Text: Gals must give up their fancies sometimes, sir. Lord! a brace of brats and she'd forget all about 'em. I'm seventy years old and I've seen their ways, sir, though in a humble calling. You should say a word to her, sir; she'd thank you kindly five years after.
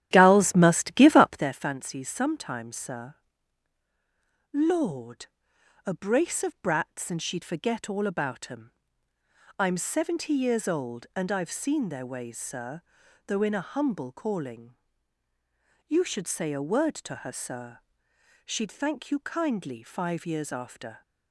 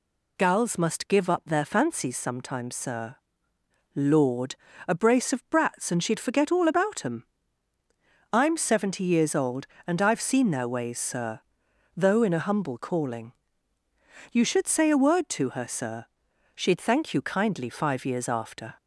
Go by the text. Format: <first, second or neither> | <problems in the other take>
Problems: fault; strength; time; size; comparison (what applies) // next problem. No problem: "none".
second | starts louder than the rest; strong; until 1.5 s; 11 dB